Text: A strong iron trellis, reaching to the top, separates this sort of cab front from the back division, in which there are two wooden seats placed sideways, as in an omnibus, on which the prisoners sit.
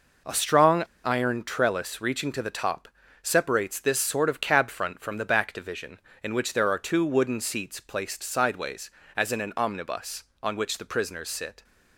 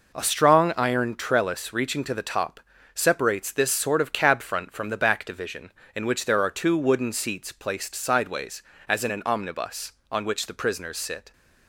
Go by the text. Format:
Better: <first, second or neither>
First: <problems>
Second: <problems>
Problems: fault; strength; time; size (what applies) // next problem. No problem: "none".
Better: second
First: pauses between "strong" and "iron"; slight; at 0.8 s; 0.19 s long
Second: none